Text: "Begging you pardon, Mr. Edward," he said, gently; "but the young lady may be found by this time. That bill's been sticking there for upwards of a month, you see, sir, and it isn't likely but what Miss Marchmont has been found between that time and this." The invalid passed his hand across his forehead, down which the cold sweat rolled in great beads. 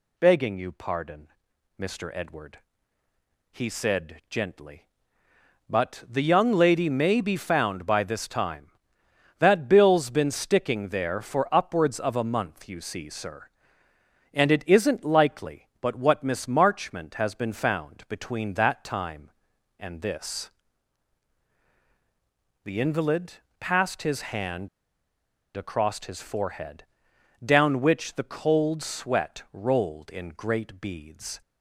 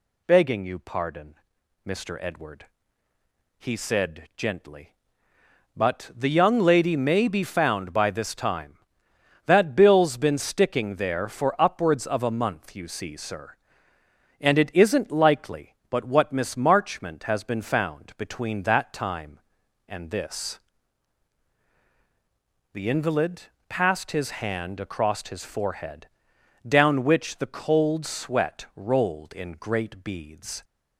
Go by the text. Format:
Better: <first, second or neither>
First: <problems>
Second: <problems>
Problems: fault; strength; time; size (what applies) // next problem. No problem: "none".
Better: second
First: pauses between "invalid" and "passed"; slight; at 23.3 s; 0.24 s long // pauses between "hand" and "across"; noticeable; at 24.6 s; 0.87 s long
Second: pauses between "invalid" and "passed"; slight; at 23.4 s; 0.24 s long